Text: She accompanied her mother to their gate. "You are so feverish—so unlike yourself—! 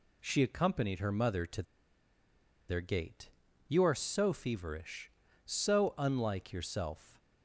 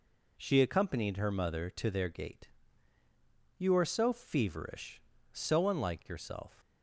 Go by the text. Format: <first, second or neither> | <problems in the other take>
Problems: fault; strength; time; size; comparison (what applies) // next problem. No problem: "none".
second | pauses between "to" and "their"; at 1.6 s; 1.0 s long